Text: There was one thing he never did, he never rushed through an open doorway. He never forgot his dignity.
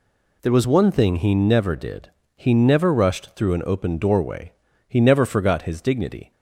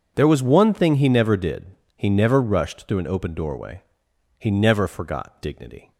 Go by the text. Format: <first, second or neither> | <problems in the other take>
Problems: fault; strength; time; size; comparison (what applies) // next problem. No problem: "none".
first | skips "his"; at 5.4 s